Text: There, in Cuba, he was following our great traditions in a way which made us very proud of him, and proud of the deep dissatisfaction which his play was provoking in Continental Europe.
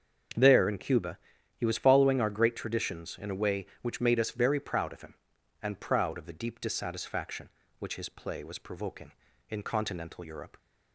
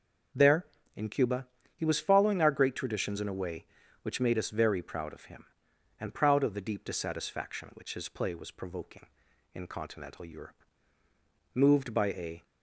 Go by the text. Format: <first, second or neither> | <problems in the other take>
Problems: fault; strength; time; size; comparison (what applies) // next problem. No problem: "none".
first | starts louder than the rest; noticeable; until 1.9 s; 6 dB; also in the first // goes on to say "Moved by a"; noticeable; from 11.5 s on; 0.90 s long